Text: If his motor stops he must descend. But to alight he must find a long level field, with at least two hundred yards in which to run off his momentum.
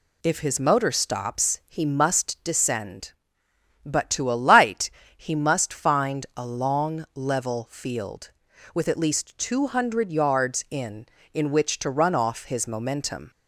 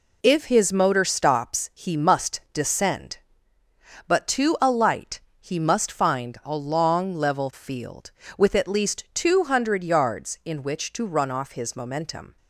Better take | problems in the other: second | pauses between "alight" and "he"; slight; at 4.9 s; 0.26 s long; slight in the second // says "in" twice; at 11.3 s

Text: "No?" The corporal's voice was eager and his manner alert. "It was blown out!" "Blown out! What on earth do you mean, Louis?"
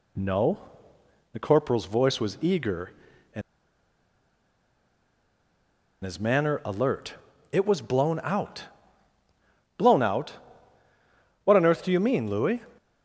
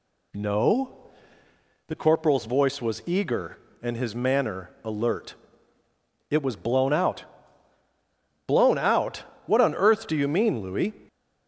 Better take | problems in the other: second | pauses between "and" and "his"; strong; at 3.4 s; 2.6 s long

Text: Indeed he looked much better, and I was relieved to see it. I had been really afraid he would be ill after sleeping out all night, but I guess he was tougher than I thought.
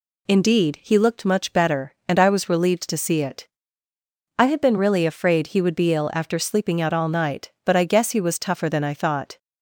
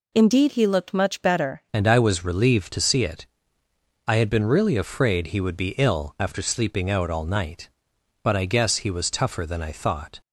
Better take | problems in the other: first | changes voice at "and"; from 1.7 s on; 8.4 s long

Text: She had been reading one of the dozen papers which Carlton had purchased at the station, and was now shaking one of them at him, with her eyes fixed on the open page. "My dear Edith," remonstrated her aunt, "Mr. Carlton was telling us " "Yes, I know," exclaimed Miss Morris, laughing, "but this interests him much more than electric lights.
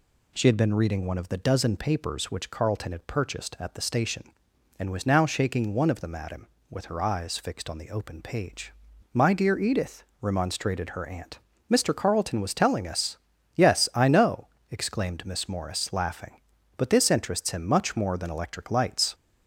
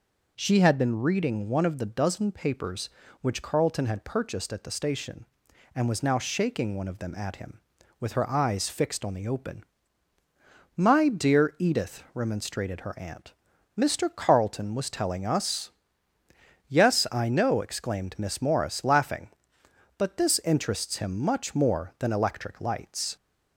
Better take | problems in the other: first | skips "page"; at 10.1 s

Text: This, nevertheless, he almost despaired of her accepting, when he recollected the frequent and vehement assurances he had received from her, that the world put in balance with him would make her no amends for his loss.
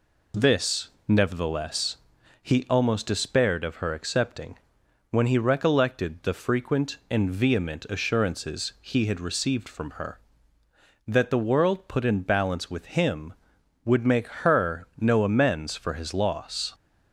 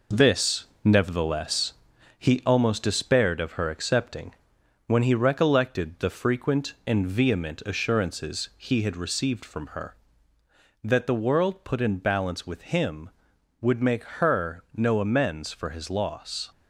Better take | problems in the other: first | gets quieter; noticeable; throughout; 5 dB // pauses between "make" and "her"; slight; at 14.0 s; 0.16 s long; slight in the first

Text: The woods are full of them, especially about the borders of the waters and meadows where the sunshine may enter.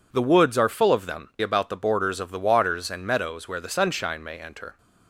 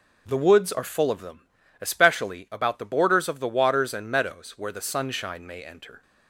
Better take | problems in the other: second | skips "especially"; at 1.3 s

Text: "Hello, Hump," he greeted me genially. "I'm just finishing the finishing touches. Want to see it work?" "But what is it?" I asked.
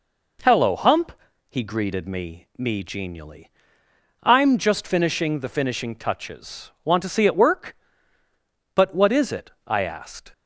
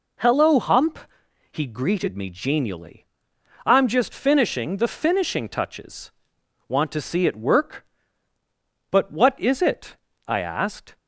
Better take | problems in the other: second | says "me" twice; at 2.5 s

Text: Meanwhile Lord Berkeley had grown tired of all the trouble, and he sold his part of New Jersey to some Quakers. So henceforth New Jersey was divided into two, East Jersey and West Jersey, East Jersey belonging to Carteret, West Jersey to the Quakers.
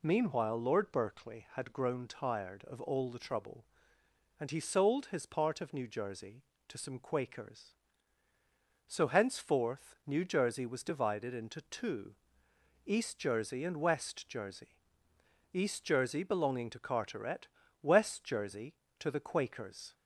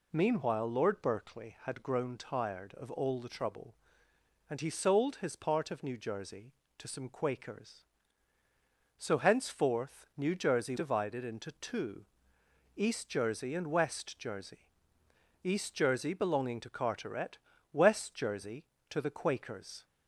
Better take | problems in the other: first | skips "was"; at 10.7 s

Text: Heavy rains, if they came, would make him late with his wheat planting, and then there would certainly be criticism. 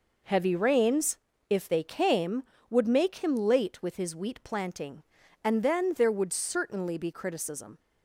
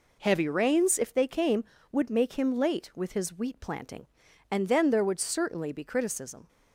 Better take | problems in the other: neither | none

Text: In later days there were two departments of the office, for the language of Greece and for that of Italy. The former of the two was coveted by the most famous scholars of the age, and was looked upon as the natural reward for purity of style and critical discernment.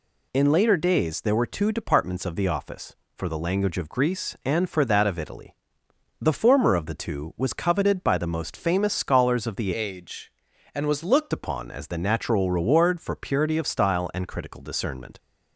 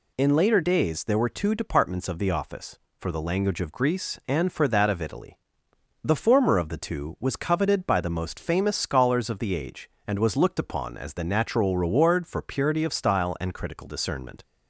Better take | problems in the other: second | changes voice from "age" to "looked"; from 9.7 to 11.3 s; 1.6 s long

